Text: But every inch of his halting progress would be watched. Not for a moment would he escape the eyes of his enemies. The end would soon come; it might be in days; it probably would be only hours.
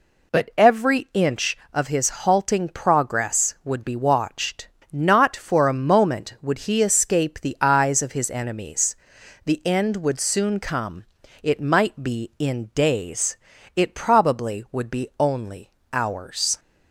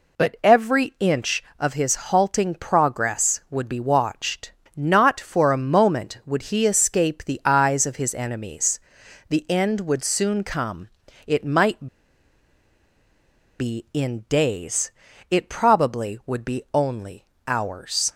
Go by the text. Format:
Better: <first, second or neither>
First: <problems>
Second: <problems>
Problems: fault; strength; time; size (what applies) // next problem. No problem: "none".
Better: first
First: pauses between "only" and "hours"; slight; at 15.7 s; 0.22 s long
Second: pauses between "might" and "be"; strong; at 11.8 s; 1.7 s long // pauses between "only" and "hours"; slight; at 17.2 s; 0.22 s long